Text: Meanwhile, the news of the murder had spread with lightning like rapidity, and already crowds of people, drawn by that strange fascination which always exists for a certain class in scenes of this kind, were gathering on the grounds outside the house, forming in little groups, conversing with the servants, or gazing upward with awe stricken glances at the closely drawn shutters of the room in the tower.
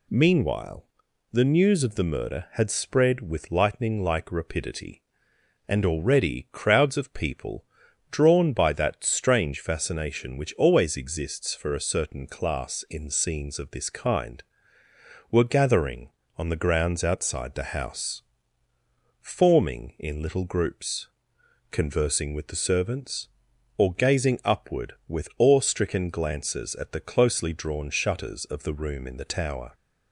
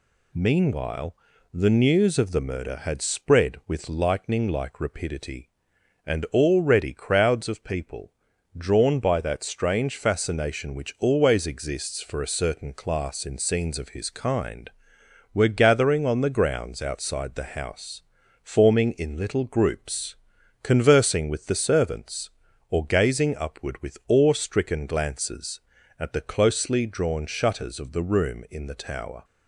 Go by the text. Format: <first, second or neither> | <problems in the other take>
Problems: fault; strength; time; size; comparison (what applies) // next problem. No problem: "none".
first | says "his" for "this"; at 13.8 s